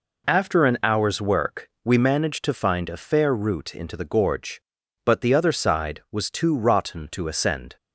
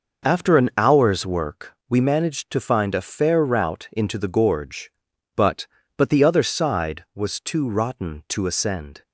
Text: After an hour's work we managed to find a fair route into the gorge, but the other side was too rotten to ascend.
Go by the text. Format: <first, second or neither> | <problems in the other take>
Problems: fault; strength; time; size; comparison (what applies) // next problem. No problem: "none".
first | pauses between "work" and "we"; slight; at 1.7 s; 0.16 s long; slight in the first // says "but" twice; at 5.9 s